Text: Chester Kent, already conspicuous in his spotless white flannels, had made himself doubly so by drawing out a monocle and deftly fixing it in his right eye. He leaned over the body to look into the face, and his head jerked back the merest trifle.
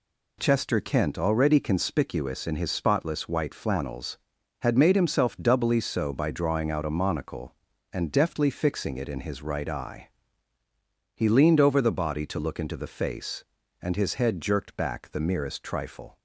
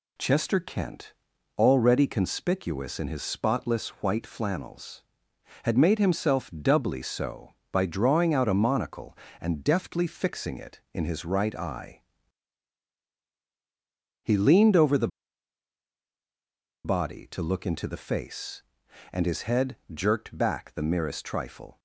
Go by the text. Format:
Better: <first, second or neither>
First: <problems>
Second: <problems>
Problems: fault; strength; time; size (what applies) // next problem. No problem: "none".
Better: first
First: none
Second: pauses between "the" and "body"; strong; at 15.0 s; 1.7 s long // pauses between "head" and "jerked"; slight; at 19.7 s; 0.18 s long